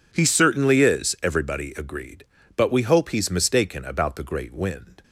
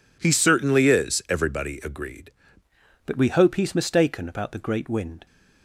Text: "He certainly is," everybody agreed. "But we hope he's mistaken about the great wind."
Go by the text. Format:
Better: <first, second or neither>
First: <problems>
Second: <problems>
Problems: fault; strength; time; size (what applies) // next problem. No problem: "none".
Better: first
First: none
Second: changes voice at "But"; from 3.0 s on; 2.2 s long